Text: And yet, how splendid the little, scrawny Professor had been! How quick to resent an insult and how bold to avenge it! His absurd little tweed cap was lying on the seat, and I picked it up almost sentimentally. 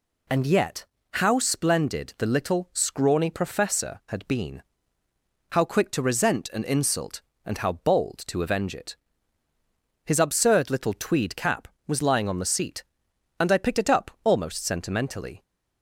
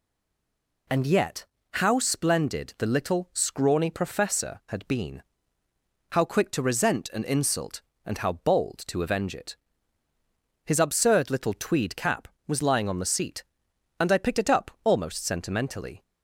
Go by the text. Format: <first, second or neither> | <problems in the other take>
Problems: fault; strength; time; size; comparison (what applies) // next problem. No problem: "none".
first | stays silent before the first word; slight; until 0.8 s; 0.8 s long